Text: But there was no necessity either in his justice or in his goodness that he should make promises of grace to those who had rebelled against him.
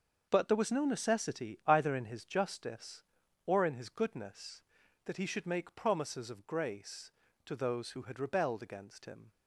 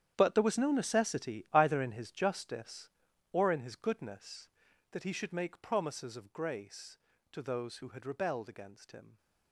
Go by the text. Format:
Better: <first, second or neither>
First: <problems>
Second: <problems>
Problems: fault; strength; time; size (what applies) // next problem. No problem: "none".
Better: first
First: starts louder than the rest; until 1.3 s; 6.5 dB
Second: gets quieter; strong; throughout; 15.5 dB // starts louder than the rest; strong; until 1.1 s; 9.5 dB